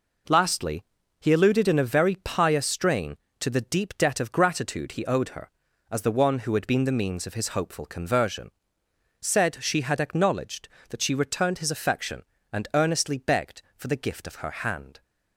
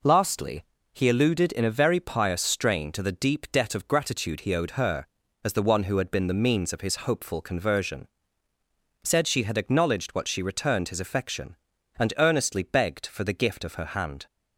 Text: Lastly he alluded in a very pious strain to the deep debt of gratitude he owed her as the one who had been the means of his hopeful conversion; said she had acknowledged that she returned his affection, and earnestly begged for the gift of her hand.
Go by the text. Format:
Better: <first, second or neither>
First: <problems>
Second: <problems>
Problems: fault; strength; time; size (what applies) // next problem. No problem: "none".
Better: first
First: pauses between "Lastly" and "he"; at 0.8 s; 0.38 s long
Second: pauses between "Lastly" and "he"; slight; at 0.6 s; 0.28 s long // says "what" for "that"; at 10.1 s